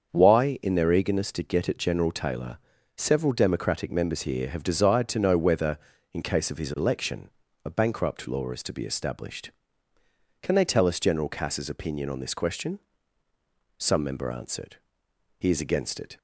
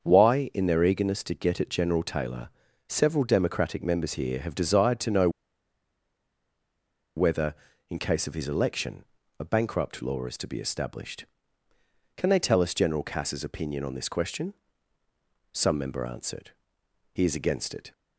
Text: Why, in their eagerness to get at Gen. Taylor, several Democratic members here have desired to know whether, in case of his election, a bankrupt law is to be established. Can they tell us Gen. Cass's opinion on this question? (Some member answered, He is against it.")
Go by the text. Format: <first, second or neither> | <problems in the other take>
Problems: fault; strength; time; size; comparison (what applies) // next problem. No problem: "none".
first | starts louder than the rest; until 1.0 s; 7 dB; also in the first // pauses between "know" and "whether"; strong; at 5.2 s; 1.8 s long